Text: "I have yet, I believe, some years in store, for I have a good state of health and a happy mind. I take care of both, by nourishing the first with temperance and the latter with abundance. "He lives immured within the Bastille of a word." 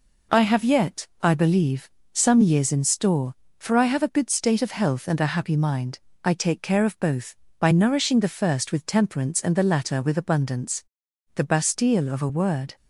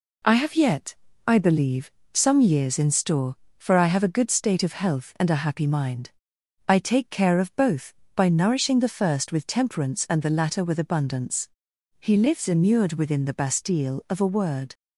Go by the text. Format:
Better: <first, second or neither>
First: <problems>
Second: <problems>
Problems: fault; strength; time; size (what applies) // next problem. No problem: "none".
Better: second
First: skips "He lives immured within"; at 11.0 s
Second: none